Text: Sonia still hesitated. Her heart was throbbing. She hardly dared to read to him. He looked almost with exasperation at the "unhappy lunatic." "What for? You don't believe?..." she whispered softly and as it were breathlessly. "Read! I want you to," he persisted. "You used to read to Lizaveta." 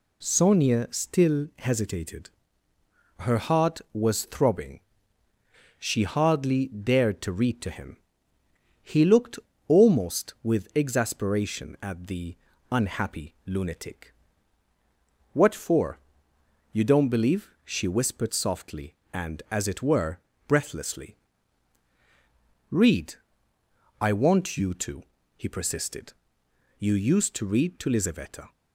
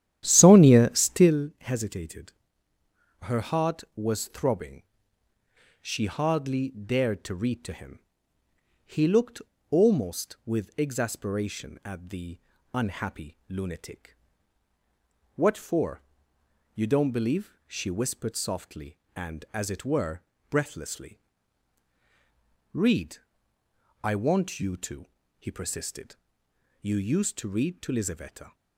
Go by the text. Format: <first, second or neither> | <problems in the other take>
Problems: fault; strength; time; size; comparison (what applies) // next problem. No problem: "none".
first | starts louder than the rest; strong; until 1.5 s; 11 dB // pauses between "looked" and "almost"; slight; at 9.4 s; 0.28 s long; slight in the first // pauses between "the" and "unhappy"; slight; at 12.3 s; 0.34 s long; slight in the first // pauses between "were" and "breathlessly"; slight; at 20.2 s; 0.26 s long; slight in the first